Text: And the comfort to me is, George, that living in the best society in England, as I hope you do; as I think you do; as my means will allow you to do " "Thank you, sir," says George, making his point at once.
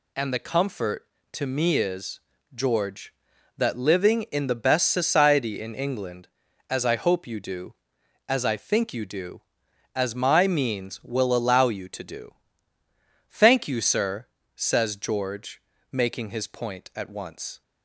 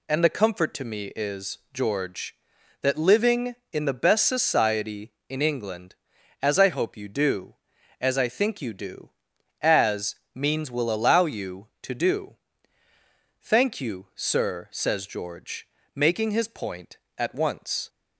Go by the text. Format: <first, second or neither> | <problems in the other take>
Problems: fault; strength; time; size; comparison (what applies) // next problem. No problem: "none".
first | skips "my"; at 10.2 s